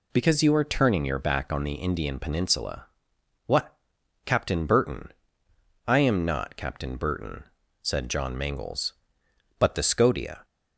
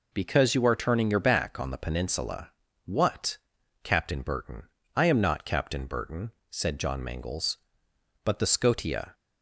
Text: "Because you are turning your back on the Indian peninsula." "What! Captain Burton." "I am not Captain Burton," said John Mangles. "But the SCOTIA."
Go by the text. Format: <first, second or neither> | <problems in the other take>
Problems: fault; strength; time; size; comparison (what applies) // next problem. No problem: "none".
first | skips "Indian"; at 1.7 s